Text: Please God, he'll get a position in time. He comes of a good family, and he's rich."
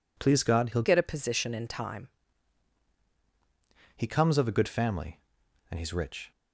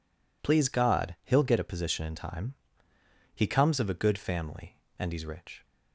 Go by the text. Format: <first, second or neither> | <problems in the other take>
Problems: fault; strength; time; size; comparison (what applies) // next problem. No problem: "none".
second | changes voice from "get" to "time"; from 0.8 to 2.0 s; 1.2 s long